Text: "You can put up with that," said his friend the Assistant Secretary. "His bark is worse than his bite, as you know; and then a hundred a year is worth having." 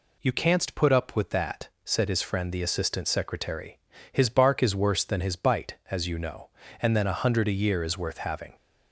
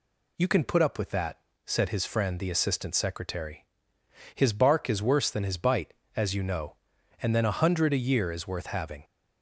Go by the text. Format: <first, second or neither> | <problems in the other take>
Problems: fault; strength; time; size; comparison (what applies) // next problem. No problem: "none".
second | says "canst" for "can"; at 0.3 s